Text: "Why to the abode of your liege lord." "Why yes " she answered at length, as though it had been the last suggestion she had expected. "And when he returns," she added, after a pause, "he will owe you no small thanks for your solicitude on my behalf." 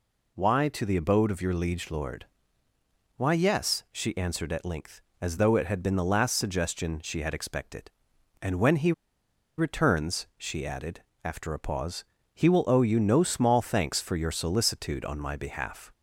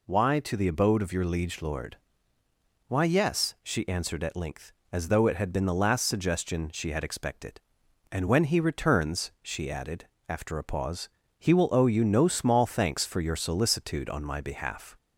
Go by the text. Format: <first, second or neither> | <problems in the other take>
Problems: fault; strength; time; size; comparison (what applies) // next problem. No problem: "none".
second | pauses between "he" and "returns"; noticeable; at 8.9 s; 0.66 s long